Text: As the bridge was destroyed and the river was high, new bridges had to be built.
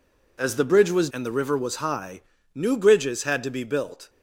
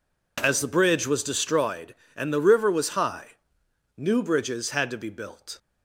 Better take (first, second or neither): second